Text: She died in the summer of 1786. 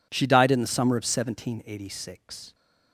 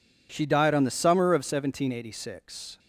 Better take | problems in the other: first | says "on" for "in"; at 0.7 s

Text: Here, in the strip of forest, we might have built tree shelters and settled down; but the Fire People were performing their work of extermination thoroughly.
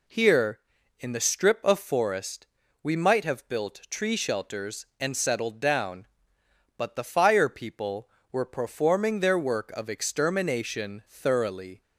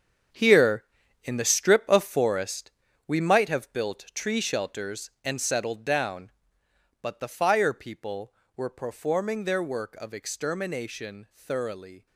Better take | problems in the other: first | gets quieter; strong; throughout; 12 dB

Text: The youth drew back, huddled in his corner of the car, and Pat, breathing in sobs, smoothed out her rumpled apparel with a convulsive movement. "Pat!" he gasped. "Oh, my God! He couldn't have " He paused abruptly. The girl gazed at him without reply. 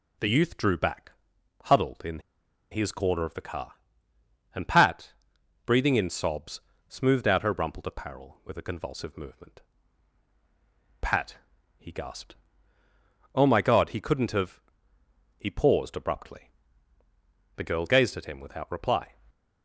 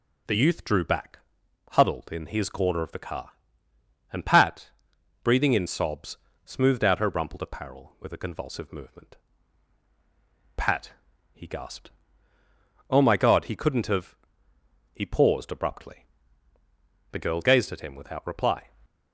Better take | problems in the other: second | pauses between "in" and "his"; noticeable; at 2.2 s; 0.50 s long

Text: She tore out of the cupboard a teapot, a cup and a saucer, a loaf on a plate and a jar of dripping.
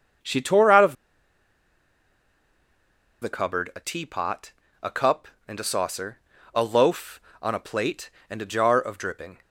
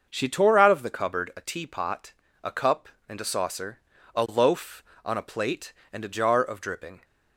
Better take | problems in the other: second | starts louder than the rest; until 3.5 s; 6 dB; noticeable in the second // pauses between "of" and "the"; strong; at 0.9 s; 2.2 s long

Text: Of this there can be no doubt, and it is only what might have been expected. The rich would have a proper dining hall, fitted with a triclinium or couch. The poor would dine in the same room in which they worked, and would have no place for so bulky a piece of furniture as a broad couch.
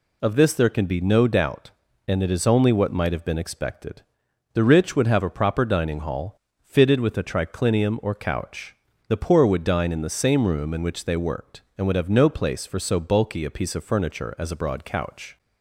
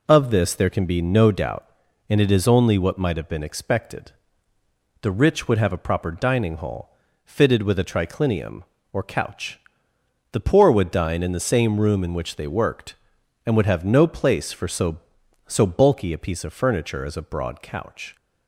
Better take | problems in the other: first | says "so" twice; at 15.4 s

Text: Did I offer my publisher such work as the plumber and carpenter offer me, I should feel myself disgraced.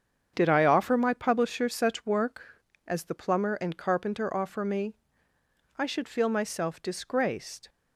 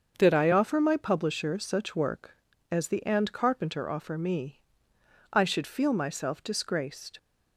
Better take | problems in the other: first | starts louder than the rest; until 1.2 s; 6.5 dB; strong in the first // skips "plumber"; at 3.0 s

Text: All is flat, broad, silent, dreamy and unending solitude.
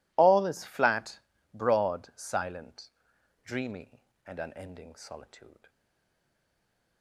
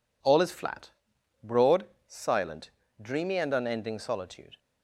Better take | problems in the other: second | stays silent after the last word; noticeable; from 5.6 s on; 1.4 s long

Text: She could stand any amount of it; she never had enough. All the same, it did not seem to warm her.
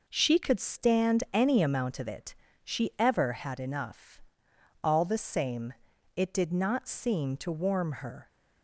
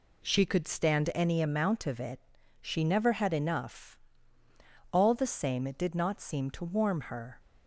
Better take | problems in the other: second | says "ever" for "never"; at 2.9 s

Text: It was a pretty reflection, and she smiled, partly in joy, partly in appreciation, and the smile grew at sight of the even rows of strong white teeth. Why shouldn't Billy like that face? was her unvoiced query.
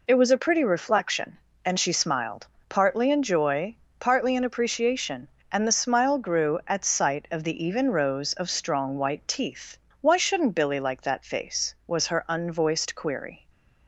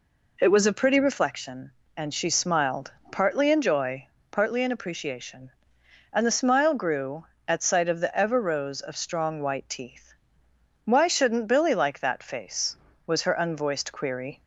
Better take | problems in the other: first | says "ever" for "even"; at 8.1 s

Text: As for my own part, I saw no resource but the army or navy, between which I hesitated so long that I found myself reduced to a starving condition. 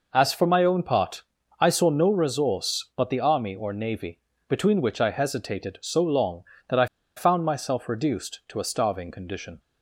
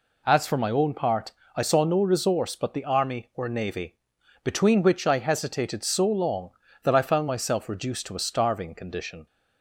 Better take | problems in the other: second | pauses between "I" and "found"; slight; at 6.8 s; 0.31 s long

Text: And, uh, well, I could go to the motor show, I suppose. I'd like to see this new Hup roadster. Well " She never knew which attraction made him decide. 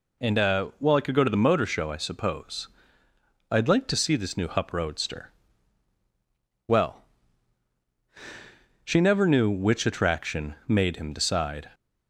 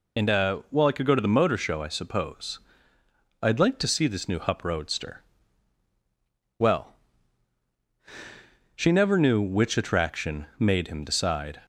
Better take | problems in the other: first | loses the start of "And"; at 0.1 s; 55 ms

